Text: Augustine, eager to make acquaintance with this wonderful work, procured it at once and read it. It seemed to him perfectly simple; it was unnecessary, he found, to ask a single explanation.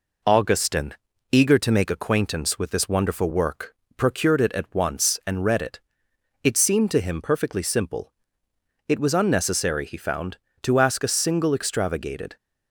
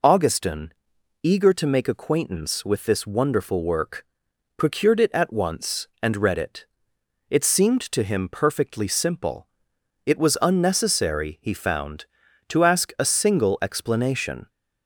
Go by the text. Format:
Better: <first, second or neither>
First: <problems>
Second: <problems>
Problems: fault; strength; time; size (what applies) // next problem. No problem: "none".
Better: second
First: says "extravagated" for "explanation"; at 11.5 s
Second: none